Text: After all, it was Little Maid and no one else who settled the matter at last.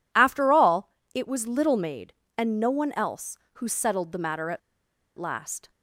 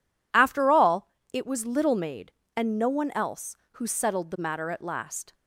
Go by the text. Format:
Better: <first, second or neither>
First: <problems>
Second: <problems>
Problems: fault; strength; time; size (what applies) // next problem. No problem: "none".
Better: second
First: pauses between "at" and "last"; noticeable; at 4.6 s; 0.58 s long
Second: none